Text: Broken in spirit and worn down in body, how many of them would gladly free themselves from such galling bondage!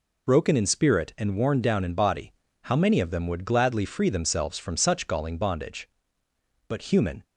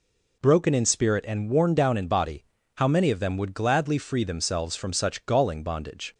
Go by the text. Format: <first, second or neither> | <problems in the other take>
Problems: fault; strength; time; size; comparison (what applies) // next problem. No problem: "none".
second | goes on to say "But human"; from 6.6 s on; 0.54 s long